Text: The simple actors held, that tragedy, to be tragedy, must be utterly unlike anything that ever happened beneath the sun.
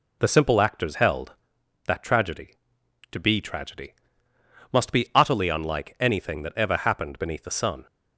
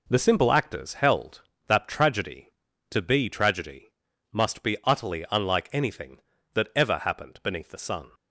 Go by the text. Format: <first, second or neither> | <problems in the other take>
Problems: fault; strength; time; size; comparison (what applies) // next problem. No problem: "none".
neither | none